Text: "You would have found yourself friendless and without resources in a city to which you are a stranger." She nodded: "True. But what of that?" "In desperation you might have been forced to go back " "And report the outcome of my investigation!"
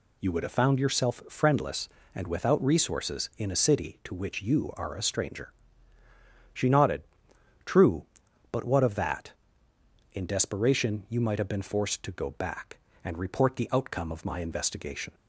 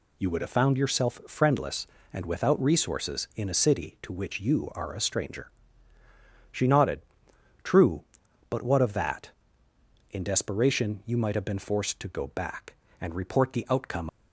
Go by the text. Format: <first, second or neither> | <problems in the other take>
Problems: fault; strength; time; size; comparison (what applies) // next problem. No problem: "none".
first | stops before "of my investigation"; at 14.0 s